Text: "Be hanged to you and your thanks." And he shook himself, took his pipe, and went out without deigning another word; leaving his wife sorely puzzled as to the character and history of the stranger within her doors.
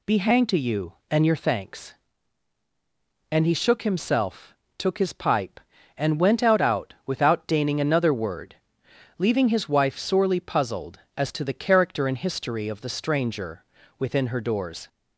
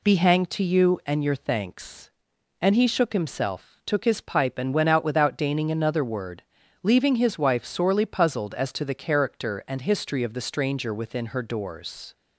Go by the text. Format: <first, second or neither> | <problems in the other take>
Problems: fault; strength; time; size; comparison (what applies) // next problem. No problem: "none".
second | says "out" twice; at 6.6 s // pauses between "stranger" and "within"; slight; at 13.6 s; 0.36 s long